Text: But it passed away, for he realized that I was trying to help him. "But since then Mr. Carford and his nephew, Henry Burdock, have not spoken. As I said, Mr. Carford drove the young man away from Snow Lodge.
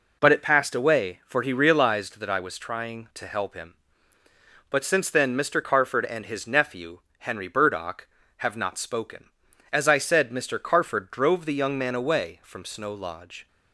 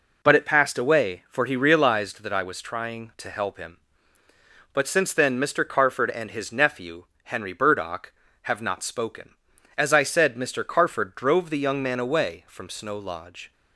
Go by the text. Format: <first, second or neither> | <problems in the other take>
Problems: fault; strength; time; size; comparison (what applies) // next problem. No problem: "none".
neither | none